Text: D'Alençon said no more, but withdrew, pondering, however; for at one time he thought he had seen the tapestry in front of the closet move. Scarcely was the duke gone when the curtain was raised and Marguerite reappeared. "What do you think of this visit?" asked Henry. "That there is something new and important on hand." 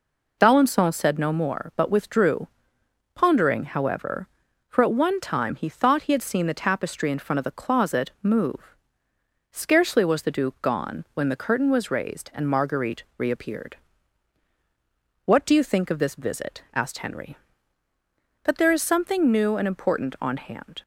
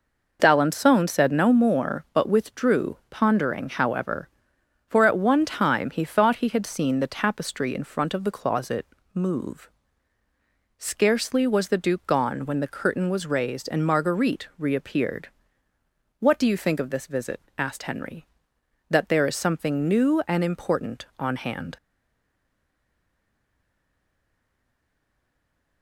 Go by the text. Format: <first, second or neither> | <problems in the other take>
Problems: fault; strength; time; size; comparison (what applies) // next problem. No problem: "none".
first | pauses between "closet" and "move"; slight; at 8.8 s; 0.26 s long // stays silent after the last word; strong; from 21.7 s on; 4.1 s long